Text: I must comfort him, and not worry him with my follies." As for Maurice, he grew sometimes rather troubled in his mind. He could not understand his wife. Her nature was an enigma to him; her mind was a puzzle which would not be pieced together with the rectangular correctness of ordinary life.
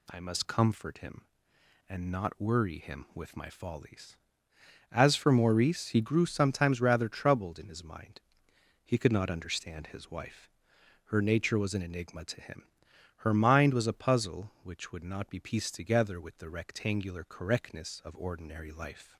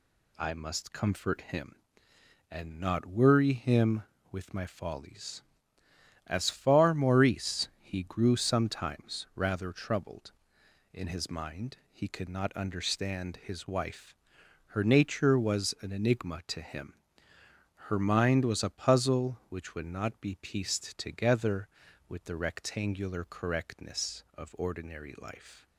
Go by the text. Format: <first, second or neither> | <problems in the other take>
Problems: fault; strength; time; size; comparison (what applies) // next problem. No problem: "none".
first | says "far" for "for"; at 6.5 s